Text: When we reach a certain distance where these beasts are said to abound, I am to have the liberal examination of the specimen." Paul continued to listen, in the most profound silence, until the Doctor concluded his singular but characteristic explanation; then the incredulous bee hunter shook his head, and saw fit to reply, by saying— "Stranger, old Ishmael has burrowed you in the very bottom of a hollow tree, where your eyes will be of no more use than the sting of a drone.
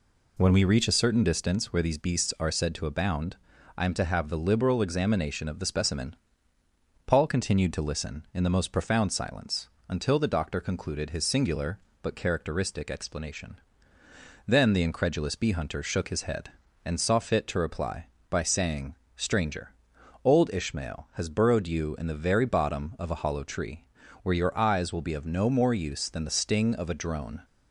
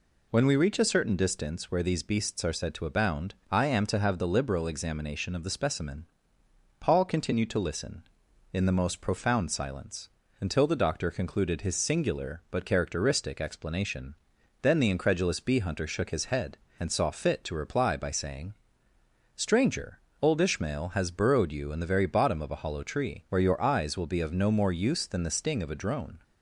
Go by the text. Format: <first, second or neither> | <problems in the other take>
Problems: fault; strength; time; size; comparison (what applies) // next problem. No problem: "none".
neither | none